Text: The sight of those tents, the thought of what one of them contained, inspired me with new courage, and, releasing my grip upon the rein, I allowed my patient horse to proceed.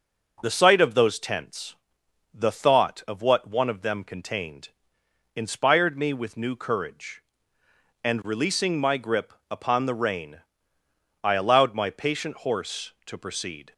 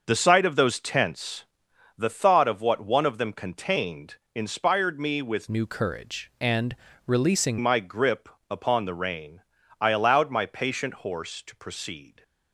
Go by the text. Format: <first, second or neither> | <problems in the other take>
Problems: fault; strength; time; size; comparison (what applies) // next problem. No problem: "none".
first | starts louder than the rest; until 1.0 s; 6.5 dB // changes voice from "new" to "releasing"; from 5.4 to 7.5 s; 2.1 s long // pauses between "grip" and "upon"; slight; at 8.2 s; 0.22 s long; slight in the first